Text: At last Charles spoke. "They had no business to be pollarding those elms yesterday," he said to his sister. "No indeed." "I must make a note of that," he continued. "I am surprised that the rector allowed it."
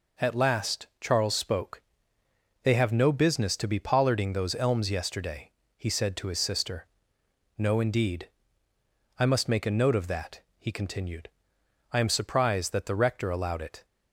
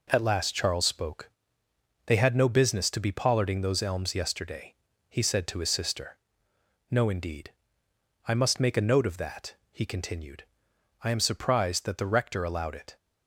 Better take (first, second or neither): second